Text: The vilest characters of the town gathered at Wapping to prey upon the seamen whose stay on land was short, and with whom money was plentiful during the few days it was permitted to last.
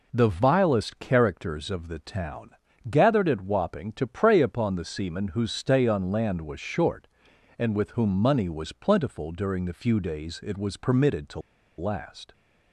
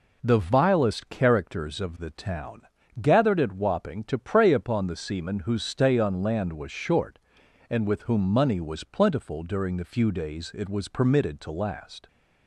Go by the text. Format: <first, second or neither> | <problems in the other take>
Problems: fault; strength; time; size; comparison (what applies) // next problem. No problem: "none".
second | pauses between "town" and "gathered"; at 2.4 s; 0.40 s long; also in the second // pauses between "to" and "last"; at 11.3 s; 0.38 s long